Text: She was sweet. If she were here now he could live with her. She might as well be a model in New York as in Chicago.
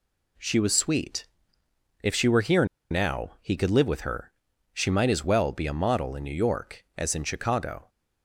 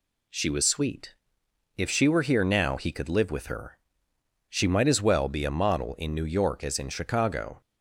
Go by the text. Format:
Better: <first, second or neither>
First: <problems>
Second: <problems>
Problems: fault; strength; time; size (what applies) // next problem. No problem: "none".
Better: second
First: pauses between "here" and "now"; slight; at 2.6 s; 0.25 s long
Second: none